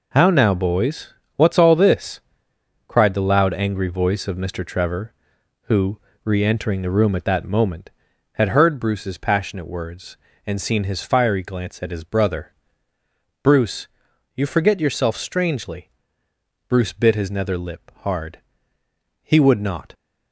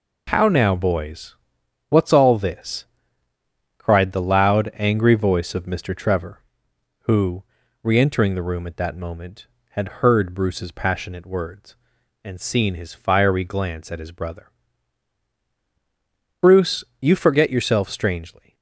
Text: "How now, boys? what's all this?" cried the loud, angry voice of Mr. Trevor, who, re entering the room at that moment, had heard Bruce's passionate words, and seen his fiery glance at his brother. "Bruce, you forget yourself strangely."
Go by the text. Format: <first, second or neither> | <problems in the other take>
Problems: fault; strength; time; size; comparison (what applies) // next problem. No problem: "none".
second | goes on to say "Bruce bit his nether lip hard He would not"; strong; from 16.6 s on; 3.2 s long